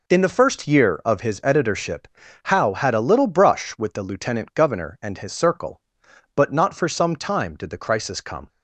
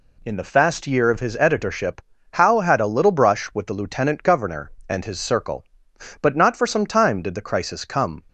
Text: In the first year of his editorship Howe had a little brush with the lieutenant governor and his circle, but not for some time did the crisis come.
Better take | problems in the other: first | says "fast" for "first"; at 0.4 s // pauses between "editorship" and "Howe"; slight; at 2.0 s; 0.32 s long; slight in the first

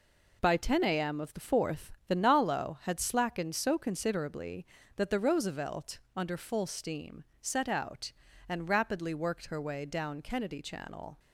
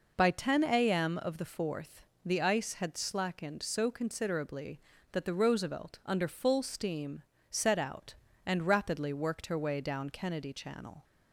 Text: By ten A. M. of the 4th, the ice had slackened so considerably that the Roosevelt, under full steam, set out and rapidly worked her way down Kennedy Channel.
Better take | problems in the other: second | says "nalo" for "ice"; at 2.1 s

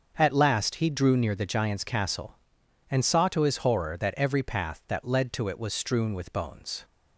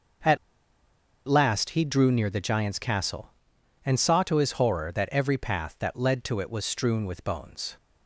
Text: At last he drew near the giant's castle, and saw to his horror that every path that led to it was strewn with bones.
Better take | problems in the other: first | starts louder than the rest; until 2.1 s; 6.5 dB; also in the first // pauses between "At" and "last"; noticeable; at 0.3 s; 0.90 s long

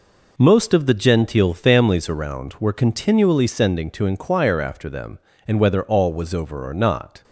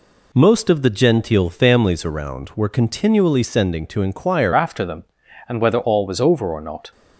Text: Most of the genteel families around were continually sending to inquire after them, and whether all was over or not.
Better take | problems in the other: first | changes voice at "after"; from 4.5 s on; 2.4 s long

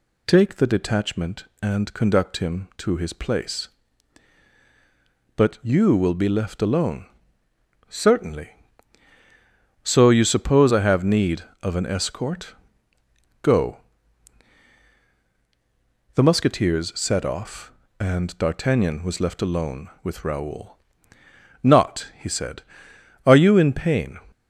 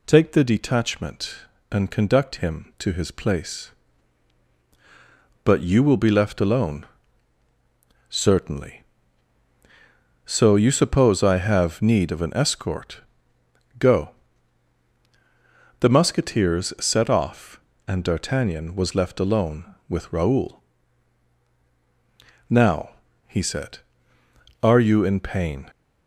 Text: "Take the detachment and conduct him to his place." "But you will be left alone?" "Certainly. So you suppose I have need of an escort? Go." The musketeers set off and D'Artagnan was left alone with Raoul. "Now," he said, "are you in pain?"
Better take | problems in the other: second | says "Not" for "Now"; at 21.6 s

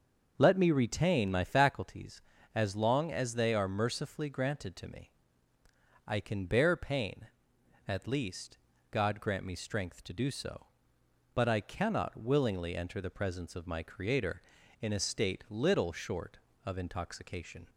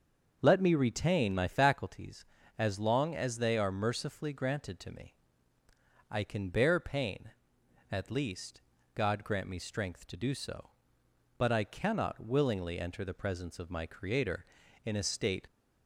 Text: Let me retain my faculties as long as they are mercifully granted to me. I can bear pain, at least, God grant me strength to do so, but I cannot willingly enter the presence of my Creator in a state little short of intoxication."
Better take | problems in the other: first | starts louder than the rest; until 1.4 s; 6.5 dB; also in the first // stops before "little short of intoxication"; at 15.4 s

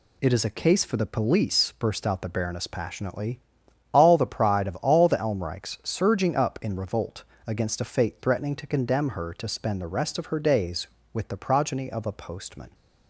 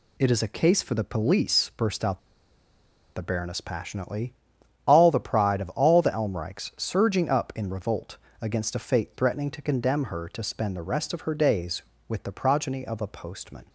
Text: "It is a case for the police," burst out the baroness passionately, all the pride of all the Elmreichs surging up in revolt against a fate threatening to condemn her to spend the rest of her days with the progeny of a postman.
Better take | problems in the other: first | pauses between "out" and "the"; noticeable; at 2.1 s; 0.97 s long // pauses between "revolt" and "against"; slight; at 8.1 s; 0.24 s long; slight in the first

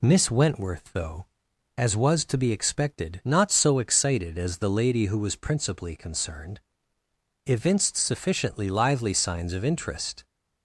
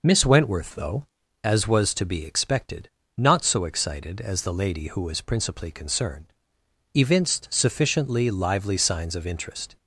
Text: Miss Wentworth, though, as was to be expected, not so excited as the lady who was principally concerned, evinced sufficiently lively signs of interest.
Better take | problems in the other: neither | none

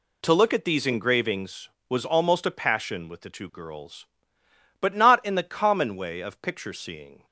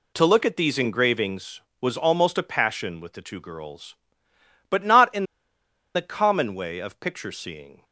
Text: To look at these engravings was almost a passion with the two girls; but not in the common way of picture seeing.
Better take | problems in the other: first | pauses between "in" and "the"; noticeable; at 5.2 s; 0.72 s long

